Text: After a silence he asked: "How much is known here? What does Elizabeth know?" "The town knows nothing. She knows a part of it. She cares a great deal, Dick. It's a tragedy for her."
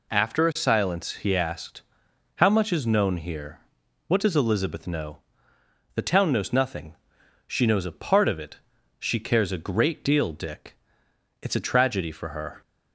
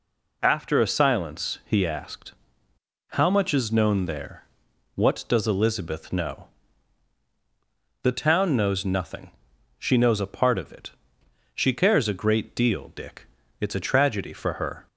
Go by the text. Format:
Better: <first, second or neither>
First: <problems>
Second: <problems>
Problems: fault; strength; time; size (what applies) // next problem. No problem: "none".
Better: first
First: none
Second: says "there" for "here"; at 4.0 s